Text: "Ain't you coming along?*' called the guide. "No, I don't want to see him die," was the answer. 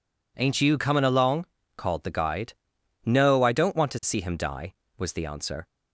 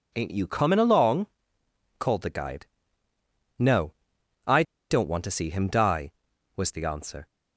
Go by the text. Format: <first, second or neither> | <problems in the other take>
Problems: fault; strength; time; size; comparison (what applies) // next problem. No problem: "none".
first | pauses between "I" and "don't"; slight; at 4.6 s; 0.27 s long